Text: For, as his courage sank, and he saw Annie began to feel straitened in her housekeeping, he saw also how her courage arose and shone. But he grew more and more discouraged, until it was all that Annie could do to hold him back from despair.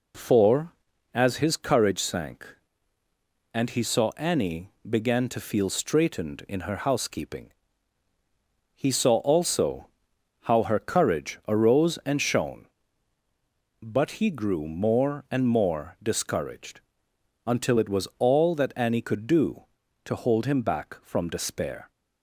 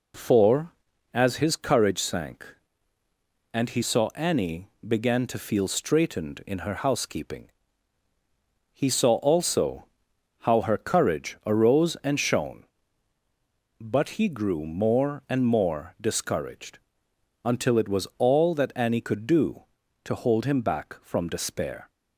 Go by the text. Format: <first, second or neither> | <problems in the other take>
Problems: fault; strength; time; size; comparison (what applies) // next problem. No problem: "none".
neither | pauses between "Annie" and "began"; slight; the same in both // pauses between "also" and "how"; noticeable; the same in both